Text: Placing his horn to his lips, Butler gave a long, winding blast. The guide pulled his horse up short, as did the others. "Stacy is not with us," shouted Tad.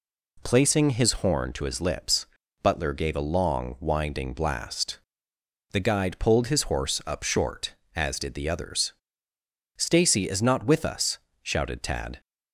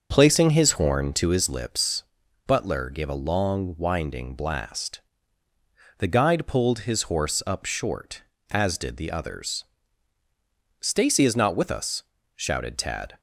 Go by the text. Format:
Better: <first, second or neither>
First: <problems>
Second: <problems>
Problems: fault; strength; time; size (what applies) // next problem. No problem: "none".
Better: first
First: none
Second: starts louder than the rest; until 1.6 s; 6.5 dB